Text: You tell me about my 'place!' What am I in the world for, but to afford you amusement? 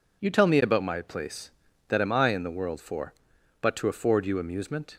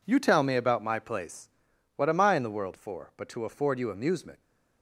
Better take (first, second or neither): second